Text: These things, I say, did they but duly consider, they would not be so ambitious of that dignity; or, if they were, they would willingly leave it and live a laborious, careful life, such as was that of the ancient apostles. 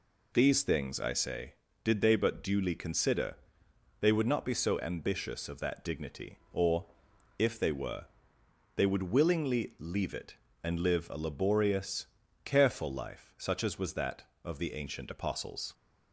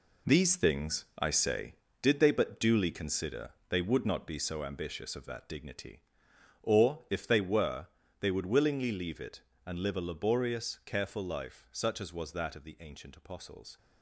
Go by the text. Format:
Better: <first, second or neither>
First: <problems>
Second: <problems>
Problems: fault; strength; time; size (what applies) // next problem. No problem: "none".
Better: first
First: none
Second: gets quieter; strong; throughout; 9.5 dB